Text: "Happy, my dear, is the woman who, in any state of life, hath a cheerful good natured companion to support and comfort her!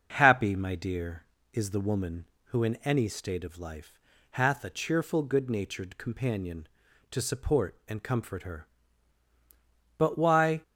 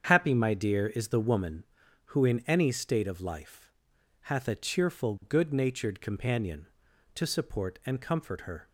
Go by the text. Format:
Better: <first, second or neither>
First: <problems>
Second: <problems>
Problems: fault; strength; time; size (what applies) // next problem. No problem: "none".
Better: second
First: starts louder than the rest; until 1.1 s; 6 dB // goes on to say "But why"; noticeable; from 9.9 s on; 0.64 s long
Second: starts louder than the rest; strong; until 1.0 s; 7.5 dB